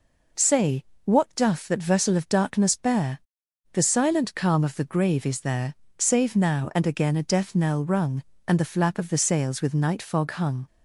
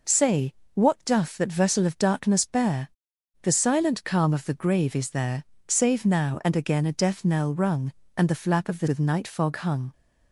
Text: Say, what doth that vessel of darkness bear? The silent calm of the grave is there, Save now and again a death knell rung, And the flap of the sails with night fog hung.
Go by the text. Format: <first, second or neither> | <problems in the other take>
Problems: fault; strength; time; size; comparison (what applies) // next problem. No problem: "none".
first | skips "sails"; at 8.8 s